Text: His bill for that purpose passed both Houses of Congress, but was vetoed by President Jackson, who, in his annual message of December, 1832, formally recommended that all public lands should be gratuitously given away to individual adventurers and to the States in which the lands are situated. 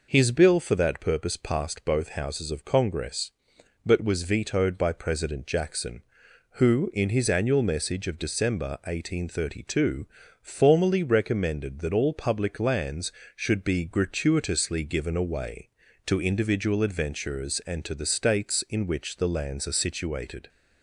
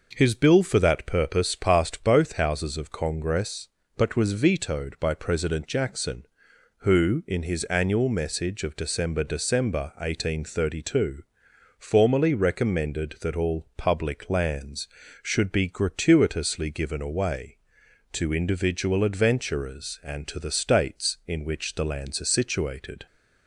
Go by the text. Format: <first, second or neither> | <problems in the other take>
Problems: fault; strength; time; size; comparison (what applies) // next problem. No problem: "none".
first | says "December" twice; at 9.2 s